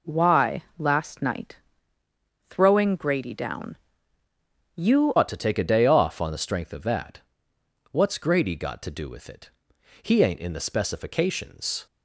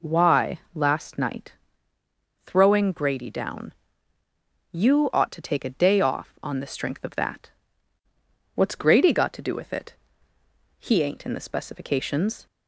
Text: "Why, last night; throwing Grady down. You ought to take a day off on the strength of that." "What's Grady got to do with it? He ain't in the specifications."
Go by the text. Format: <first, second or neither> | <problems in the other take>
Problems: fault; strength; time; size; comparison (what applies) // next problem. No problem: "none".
second | changes voice at "ought"; from 5.1 s on; 6.7 s long